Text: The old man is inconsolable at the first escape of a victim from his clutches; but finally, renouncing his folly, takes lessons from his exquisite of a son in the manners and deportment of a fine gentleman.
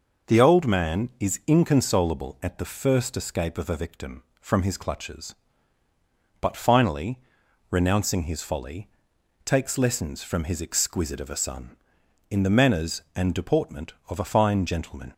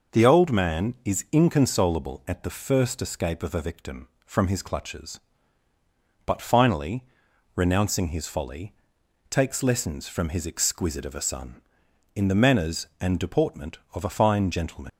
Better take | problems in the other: first | leaves "gentleman" unfinished; at 14.8 s; 80 ms

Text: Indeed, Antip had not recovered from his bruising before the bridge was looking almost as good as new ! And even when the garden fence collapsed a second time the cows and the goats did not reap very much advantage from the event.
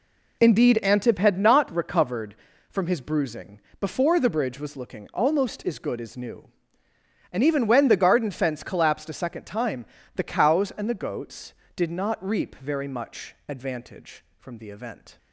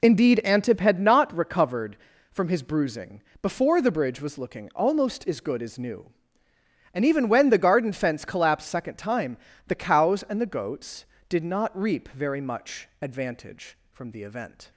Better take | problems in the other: first | pauses between "bruising" and "before"; slight; at 3.2 s; 0.22 s long; slight in the first // skips "a"; at 8.6 s // pauses between "time" and "the"; slight; at 9.3 s; 0.30 s long; slight in the first

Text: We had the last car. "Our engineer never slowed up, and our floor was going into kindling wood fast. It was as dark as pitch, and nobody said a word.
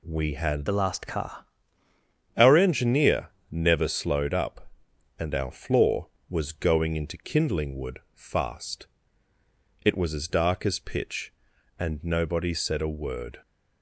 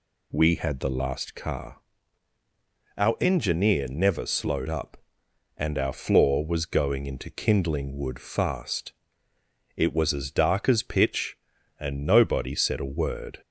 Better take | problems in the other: second | changes voice from "the" to "car"; from 0.6 to 1.4 s; 0.8 s long // pauses between "engineer" and "never"; slight; at 3.2 s; 0.22 s long // pauses between "wood" and "fast"; slight; at 7.9 s; 0.16 s long

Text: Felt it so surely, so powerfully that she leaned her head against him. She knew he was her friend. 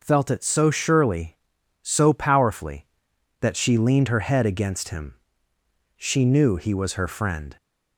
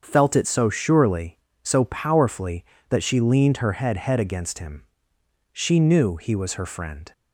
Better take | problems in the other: first | starts louder than the rest; until 1.0 s; 7 dB // says "head" twice; at 3.9 s

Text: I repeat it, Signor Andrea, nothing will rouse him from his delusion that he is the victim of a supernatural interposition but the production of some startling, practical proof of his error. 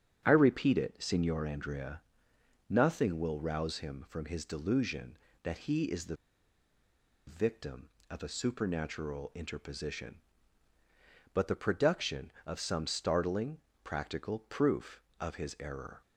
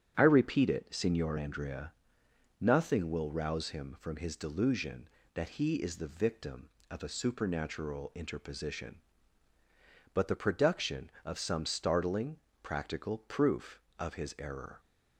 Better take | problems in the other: second | starts louder than the rest; strong; until 1.2 s; 9 dB; strong in the second // pauses between "the" and "victim"; at 6.1 s; 1.1 s long

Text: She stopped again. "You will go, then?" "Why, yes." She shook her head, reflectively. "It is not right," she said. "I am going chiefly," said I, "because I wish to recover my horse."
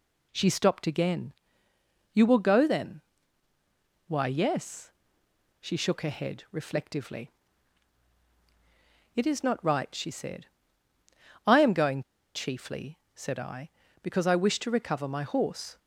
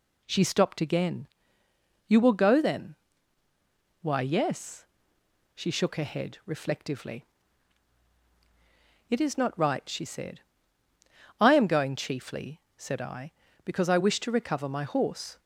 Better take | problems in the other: second | pauses between "going" and "chiefly"; slight; at 12.0 s; 0.32 s long

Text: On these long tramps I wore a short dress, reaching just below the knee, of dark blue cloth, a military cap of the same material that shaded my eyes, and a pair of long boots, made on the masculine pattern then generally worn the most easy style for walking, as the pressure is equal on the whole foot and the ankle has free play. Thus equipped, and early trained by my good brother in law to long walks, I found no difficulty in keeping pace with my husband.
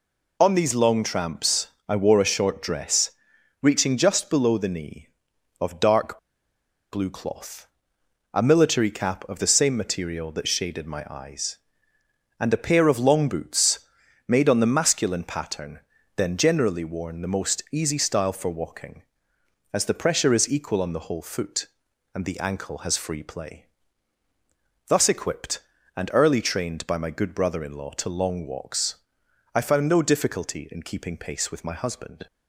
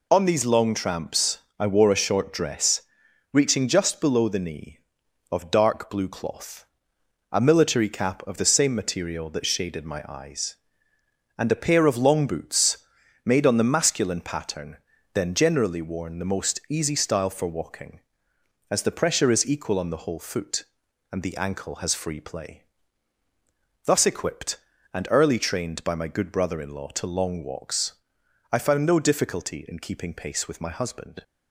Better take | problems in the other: second | pauses between "tramps" and "I"; slight; at 1.6 s; 0.20 s long; slight in the second // pauses between "dark" and "blue"; noticeable; at 6.1 s; 0.74 s long // pauses between "pattern" and "then"; at 15.7 s; 0.38 s long; also in the second

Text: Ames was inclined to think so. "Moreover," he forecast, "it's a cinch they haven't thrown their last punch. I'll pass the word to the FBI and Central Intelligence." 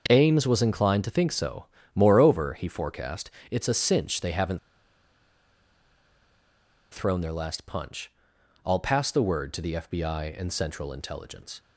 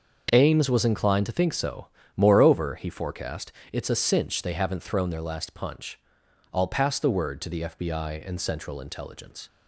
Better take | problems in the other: second | starts louder than the rest; until 1.0 s; 6.5 dB; also in the second // pauses between "haven't" and "thrown"; strong; at 4.5 s; 2.3 s long

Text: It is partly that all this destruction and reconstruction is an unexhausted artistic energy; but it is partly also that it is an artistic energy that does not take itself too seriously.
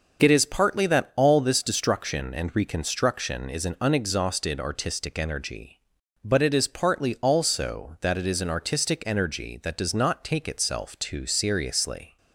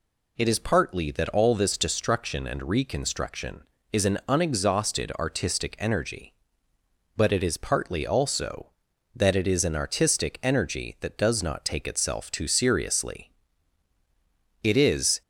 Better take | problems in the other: first | goes on to say "It is"; from 14.6 s on; 0.58 s long

